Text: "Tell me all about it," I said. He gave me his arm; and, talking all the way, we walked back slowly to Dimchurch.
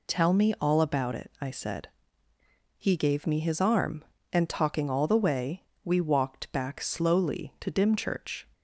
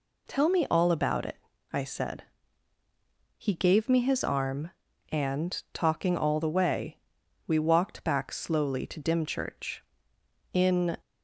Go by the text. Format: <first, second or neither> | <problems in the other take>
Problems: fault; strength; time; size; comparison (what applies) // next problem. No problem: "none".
first | goes on to say "In"; slight; from 10.5 s on; 0.44 s long